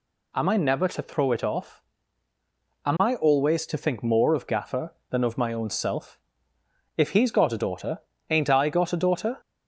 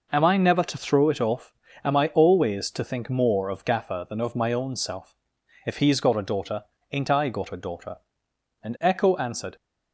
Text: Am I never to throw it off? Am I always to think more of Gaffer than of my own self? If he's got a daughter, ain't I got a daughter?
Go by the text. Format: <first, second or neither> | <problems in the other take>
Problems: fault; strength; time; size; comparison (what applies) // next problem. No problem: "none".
first | goes on to say "And echo answered"; noticeable; from 8.6 s on; 0.91 s long